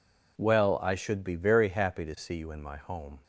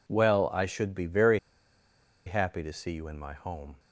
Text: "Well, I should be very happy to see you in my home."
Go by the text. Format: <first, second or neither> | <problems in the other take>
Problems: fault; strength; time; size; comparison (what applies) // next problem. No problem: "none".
first | pauses between "very" and "happy"; noticeable; at 1.3 s; 0.87 s long